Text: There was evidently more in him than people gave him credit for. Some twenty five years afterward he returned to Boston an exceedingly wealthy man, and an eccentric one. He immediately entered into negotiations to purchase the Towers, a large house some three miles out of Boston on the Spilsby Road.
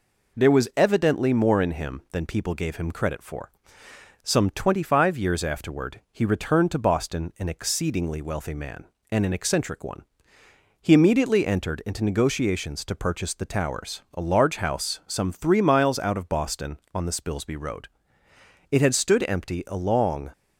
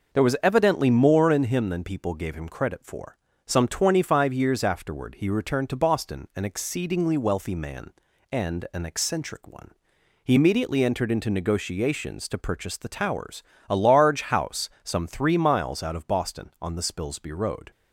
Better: second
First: goes on to say "It had stood empty a long"; from 18.7 s on; 1.6 s long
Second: none

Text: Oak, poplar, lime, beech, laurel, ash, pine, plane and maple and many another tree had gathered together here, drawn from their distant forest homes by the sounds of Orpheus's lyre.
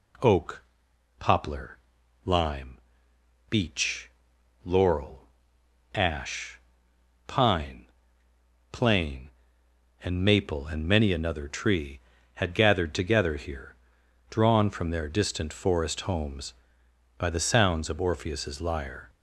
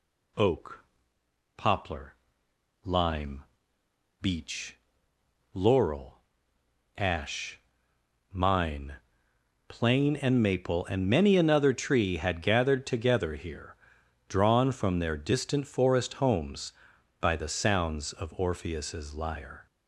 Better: first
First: none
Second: says "mine" for "pine"; at 8.3 s

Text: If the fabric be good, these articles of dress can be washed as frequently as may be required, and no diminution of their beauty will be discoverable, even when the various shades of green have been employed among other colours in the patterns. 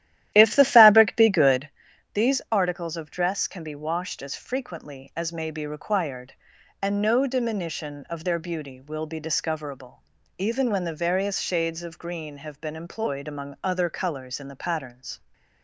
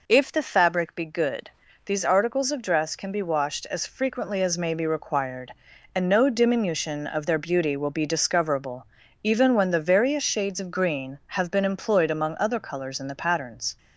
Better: second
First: starts louder than the rest; strong; until 1.7 s; 13 dB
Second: none

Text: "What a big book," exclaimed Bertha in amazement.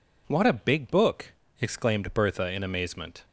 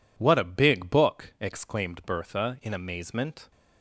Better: neither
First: none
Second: none

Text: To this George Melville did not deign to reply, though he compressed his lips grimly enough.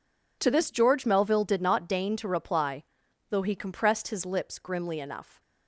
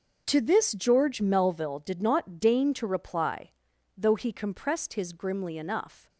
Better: first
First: none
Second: starts louder than the rest; until 1.2 s; 6.5 dB // skips "lips"; at 5.1 s

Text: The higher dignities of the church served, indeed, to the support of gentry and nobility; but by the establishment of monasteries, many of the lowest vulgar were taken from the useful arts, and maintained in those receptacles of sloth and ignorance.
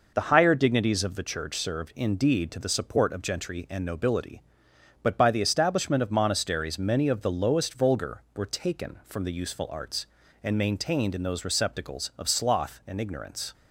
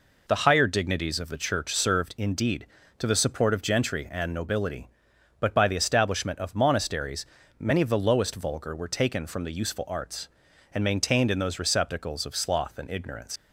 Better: first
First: none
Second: leaves "ignorance" unfinished; at 13.3 s; 90 ms

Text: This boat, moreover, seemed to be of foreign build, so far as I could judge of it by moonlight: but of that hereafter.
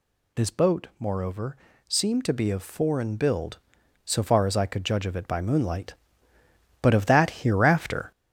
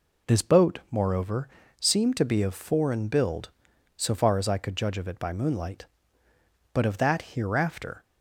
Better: second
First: gets louder; noticeable; throughout; 5.5 dB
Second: none

